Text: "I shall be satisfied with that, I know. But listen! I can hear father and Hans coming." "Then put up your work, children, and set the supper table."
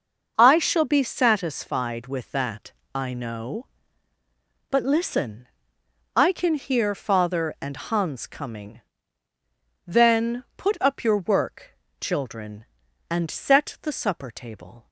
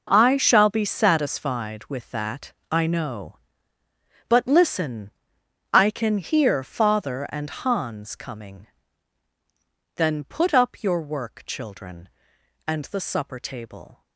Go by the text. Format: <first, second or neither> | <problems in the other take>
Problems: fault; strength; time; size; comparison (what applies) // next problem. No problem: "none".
first | skips "set"; at 12.8 s